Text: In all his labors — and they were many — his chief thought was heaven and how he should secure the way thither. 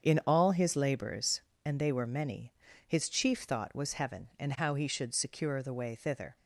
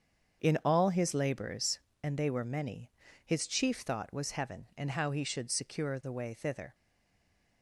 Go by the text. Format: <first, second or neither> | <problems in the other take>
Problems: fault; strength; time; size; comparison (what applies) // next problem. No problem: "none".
first | starts louder than the rest; strong; until 1.4 s; 7 dB; strong in the first // stays silent after the last word; slight; from 6.7 s on; 0.9 s long